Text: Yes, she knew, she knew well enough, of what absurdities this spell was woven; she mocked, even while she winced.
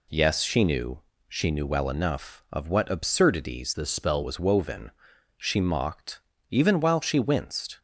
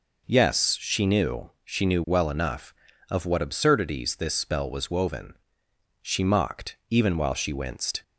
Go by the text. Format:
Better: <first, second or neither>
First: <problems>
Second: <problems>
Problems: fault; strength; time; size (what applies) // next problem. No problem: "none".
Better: second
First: changes voice from "this" to "spell"; from 3.7 to 4.2 s; 0.5 s long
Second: none